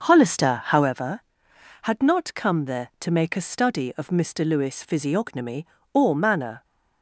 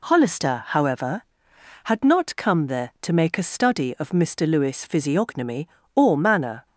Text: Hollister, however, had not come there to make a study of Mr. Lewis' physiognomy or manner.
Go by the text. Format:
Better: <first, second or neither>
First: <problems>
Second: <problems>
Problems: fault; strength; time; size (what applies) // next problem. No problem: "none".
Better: second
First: starts louder than the rest; until 0.9 s; 6.5 dB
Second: none